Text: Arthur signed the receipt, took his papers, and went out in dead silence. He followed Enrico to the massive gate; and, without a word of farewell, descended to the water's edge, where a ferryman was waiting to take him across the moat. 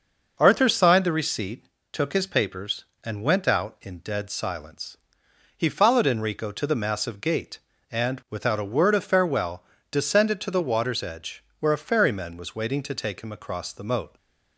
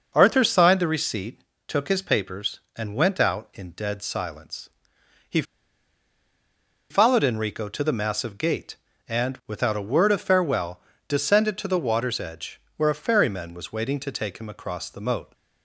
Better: first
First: starts louder than the rest; noticeable; until 1.4 s; 6 dB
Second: starts louder than the rest; noticeable; until 1.1 s; 6 dB // pauses between "He" and "followed"; strong; at 5.4 s; 1.4 s long

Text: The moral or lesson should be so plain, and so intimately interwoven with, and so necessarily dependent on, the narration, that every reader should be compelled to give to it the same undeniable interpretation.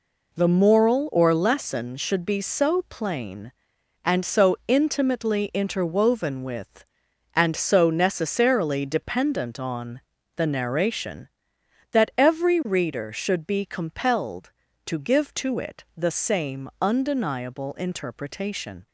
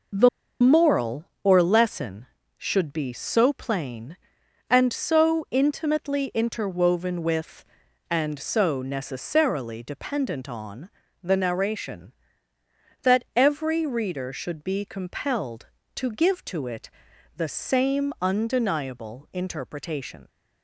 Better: first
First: none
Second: pauses between "The" and "moral"; slight; at 0.2 s; 0.32 s long // pauses between "it" and "the"; at 16.9 s; 0.44 s long

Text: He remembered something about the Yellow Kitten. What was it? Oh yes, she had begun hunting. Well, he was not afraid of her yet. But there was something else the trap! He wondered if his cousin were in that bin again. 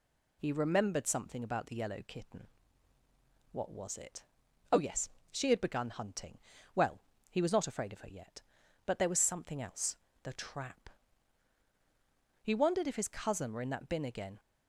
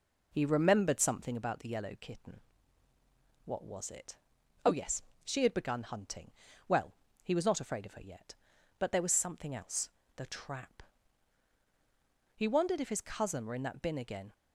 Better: first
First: pauses between "else" and "the"; slight; at 9.9 s; 0.26 s long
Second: starts louder than the rest; noticeable; until 1.4 s; 4.5 dB // pauses between "else" and "the"; slight; at 9.9 s; 0.26 s long

